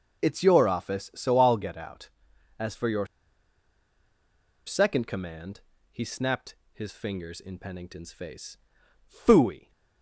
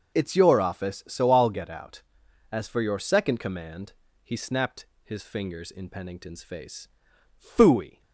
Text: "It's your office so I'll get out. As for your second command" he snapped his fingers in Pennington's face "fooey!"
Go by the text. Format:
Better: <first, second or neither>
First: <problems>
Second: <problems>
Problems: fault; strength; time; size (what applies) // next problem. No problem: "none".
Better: second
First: pauses between "your" and "second"; strong; at 3.0 s; 1.6 s long // pauses between "command" and "he"; slight; at 5.5 s; 0.32 s long // pauses between "snapped" and "his"; slight; at 6.5 s; 0.18 s long // pauses between "face" and "fooey"; noticeable; at 8.5 s; 0.54 s long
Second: pauses between "command" and "he"; slight; at 3.9 s; 0.32 s long // pauses between "snapped" and "his"; slight; at 4.8 s; 0.18 s long // pauses between "face" and "fooey"; noticeable; at 6.8 s; 0.54 s long